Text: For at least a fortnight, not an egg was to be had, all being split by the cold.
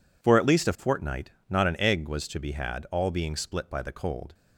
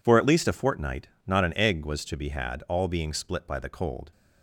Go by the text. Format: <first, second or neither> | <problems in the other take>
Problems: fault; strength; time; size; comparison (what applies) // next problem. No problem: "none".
neither | none